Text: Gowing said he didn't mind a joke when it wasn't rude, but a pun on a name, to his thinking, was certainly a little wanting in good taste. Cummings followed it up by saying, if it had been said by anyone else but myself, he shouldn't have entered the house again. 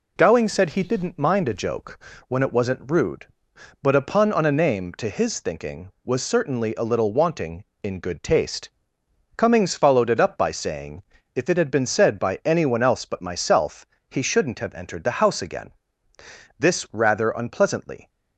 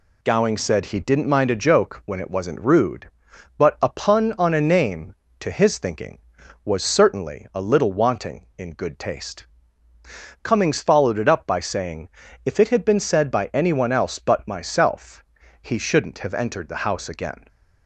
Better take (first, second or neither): second